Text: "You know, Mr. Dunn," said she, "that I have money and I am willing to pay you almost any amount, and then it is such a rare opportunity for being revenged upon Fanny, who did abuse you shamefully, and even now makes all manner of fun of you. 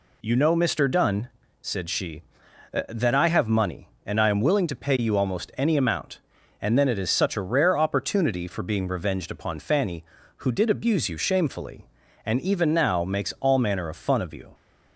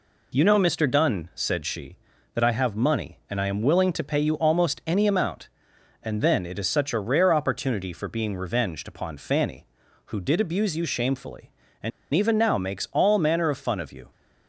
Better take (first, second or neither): first